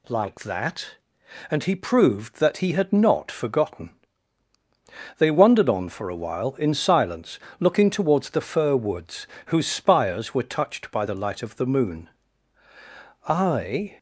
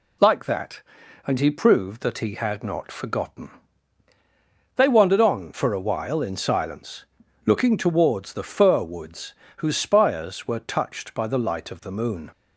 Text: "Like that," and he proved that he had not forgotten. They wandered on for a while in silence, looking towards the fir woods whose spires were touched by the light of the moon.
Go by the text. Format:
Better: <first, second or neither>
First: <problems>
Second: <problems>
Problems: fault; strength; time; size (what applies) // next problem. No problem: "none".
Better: second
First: pauses between "woods" and "whose"; slight; at 9.2 s; 0.20 s long // goes on to say "I"; noticeable; from 13.2 s on; 0.70 s long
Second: pauses between "woods" and "whose"; slight; at 9.3 s; 0.26 s long